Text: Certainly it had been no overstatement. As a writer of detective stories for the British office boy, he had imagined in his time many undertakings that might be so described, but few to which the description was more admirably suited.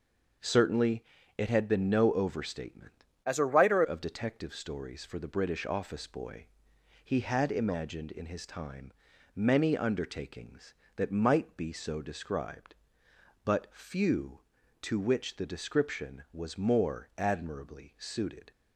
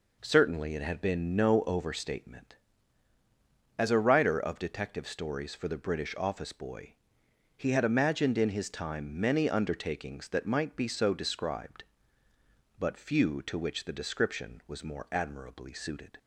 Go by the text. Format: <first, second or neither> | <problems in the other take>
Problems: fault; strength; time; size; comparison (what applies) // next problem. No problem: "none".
second | pauses between "Certainly" and "it"; slight; at 1.0 s; 0.32 s long // changes voice from "As" to "writer"; from 3.2 to 3.8 s; 0.6 s long // pauses between "time" and "many"; at 8.9 s; 0.44 s long